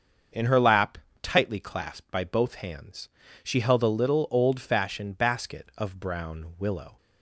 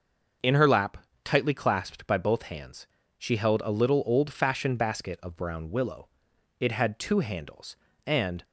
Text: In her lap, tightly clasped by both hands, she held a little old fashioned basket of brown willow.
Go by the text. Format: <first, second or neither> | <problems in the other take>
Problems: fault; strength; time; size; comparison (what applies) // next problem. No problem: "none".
first | starts louder than the rest; until 1.6 s; 6 dB; also in the first // goes on to say "It had two handles and"; strong; from 6.5 s on; 1.8 s long